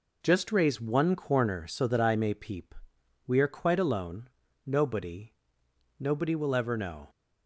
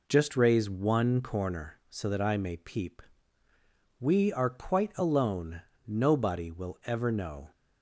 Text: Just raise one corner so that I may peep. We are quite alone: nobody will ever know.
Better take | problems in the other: second | says "nobody" twice; at 5.9 s

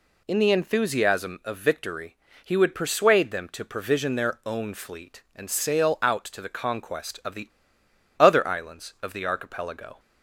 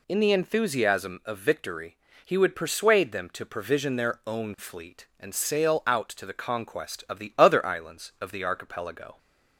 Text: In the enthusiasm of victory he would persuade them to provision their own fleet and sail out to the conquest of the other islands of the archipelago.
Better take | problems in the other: second | pauses between "victory" and "he"; slight; at 2.1 s; 0.30 s long; slight in the second // pauses between "the" and "other"; noticeable; at 7.4 s; 0.69 s long

